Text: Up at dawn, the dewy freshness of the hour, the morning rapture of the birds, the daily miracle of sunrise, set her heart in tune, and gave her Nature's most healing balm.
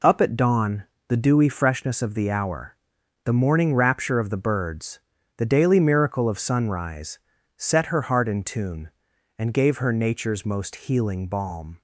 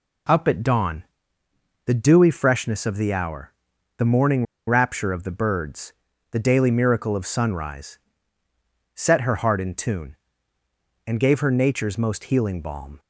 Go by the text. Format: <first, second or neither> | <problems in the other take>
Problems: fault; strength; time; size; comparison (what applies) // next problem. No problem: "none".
first | pauses between "morning" and "rapture"; slight; at 4.4 s; 0.22 s long